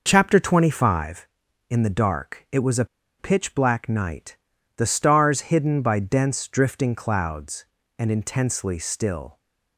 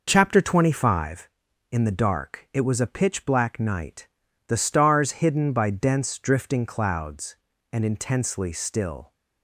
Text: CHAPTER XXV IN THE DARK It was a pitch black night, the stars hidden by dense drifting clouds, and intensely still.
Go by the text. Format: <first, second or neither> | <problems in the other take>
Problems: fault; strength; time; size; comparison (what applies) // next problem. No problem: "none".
second | pauses between "a" and "pitch"; slight; at 2.8 s; 0.33 s long